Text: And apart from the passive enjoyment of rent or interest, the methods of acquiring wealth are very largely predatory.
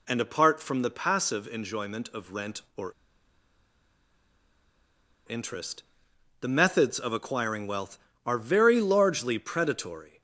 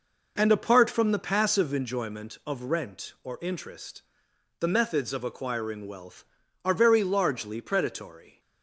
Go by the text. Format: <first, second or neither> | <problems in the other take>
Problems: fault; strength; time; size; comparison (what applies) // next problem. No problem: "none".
second | pauses between "or" and "interest"; strong; at 2.9 s; 2.3 s long